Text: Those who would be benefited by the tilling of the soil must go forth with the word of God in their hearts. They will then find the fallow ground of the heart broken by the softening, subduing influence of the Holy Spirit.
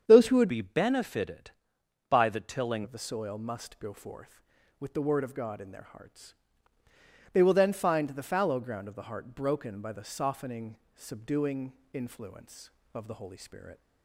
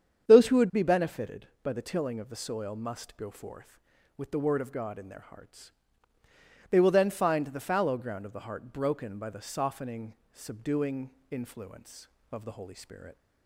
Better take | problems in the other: second | starts louder than the rest; strong; until 1.0 s; 8 dB; strong in the second // changes voice from "be" to "tilling"; from 0.4 to 2.8 s; 2.4 s long // pauses between "subduing" and "influence"; slight; at 11.7 s; 0.22 s long; slight in the second

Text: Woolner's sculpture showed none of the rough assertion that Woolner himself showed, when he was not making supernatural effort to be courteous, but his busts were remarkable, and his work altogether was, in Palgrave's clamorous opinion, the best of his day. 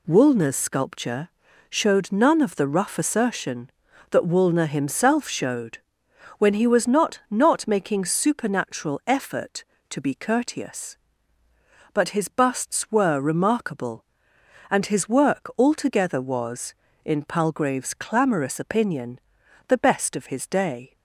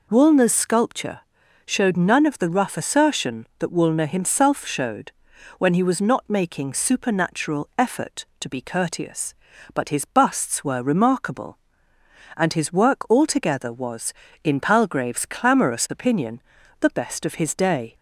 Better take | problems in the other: second | pauses between "sculpture" and "showed"; at 1.2 s; 0.38 s long; noticeable in the second // says "not" twice; at 7.3 s

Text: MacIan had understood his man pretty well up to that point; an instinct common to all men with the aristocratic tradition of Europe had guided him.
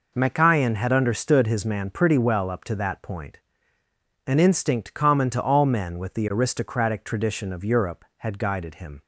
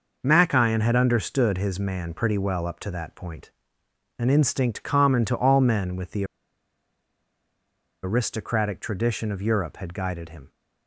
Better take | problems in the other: first | pauses between "the" and "aristocratic"; strong; at 6.2 s; 1.7 s long

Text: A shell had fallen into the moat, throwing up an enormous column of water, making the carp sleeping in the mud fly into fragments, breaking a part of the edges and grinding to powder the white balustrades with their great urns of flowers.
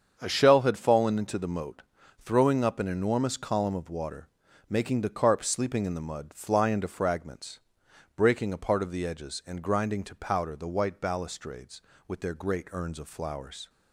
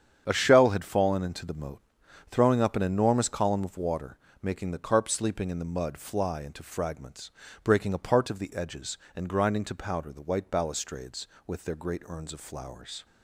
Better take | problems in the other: neither | starts louder than the rest; strong; the same in both

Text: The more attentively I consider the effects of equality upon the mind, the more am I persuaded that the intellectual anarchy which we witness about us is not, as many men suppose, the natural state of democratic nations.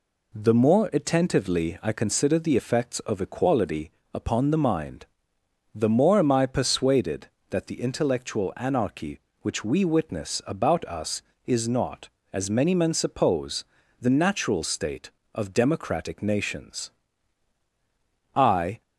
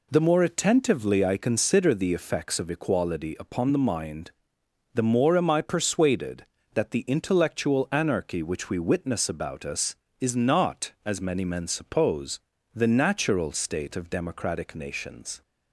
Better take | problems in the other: second | pauses between "equality" and "upon"; slight; at 3.9 s; 0.22 s long // goes on to say "I"; slight; from 18.3 s on; 0.46 s long

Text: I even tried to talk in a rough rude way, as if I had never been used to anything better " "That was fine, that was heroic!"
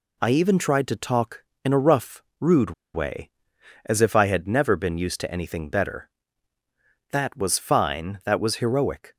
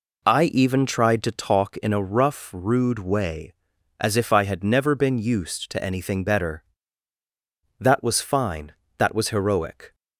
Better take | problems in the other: second | pauses between "rough" and "rude"; slight; at 2.2 s; 0.16 s long // pauses between "rude" and "way"; slight; at 2.7 s; 0.22 s long

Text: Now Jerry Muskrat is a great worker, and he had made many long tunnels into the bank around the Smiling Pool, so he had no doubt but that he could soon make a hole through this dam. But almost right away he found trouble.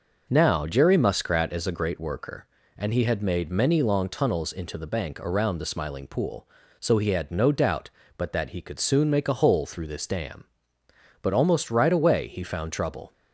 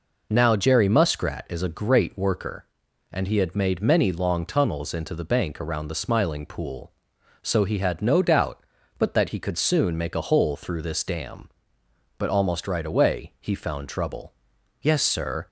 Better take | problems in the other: first | goes on to say "Yes Sir"; noticeable; from 14.8 s on; 0.66 s long

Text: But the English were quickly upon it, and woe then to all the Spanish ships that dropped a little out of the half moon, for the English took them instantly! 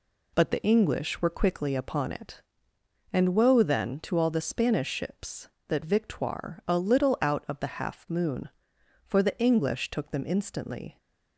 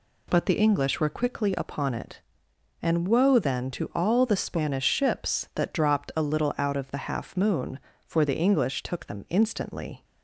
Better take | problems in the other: second | says "victoire" for "dropped"; at 5.8 s

